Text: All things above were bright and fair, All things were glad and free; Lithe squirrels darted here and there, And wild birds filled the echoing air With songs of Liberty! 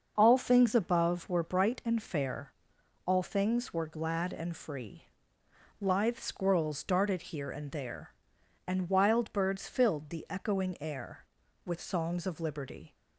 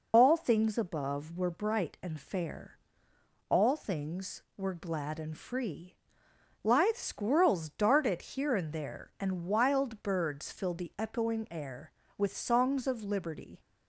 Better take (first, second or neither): first